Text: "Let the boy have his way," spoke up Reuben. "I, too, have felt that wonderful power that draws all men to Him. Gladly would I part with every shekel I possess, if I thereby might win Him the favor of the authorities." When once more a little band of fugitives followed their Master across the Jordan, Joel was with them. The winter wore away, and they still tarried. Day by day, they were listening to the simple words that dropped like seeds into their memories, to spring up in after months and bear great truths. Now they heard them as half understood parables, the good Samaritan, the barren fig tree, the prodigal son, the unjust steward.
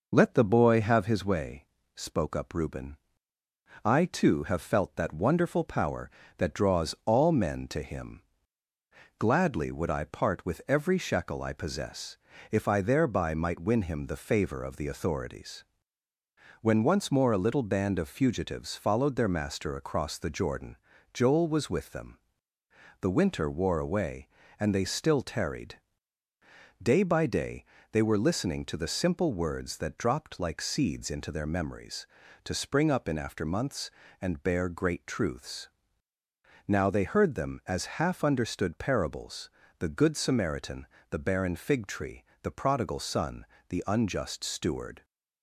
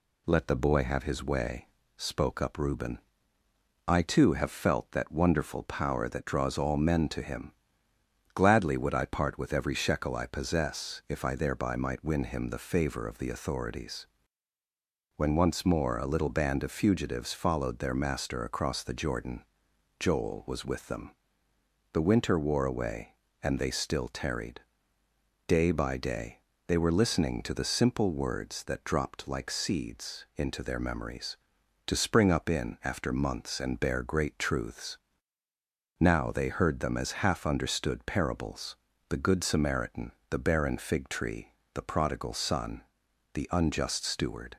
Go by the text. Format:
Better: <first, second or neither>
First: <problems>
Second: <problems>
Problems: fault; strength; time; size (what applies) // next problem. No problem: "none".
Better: neither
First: none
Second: none